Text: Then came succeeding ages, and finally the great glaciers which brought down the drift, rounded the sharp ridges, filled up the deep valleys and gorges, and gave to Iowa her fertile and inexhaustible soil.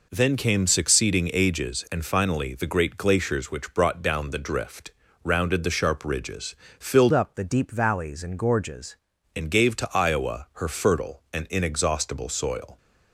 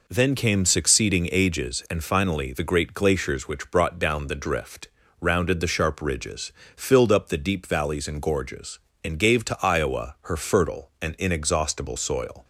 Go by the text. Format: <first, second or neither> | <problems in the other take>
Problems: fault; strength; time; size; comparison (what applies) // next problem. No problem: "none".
second | changes voice from "up" to "gorges"; from 7.1 to 8.9 s; 1.8 s long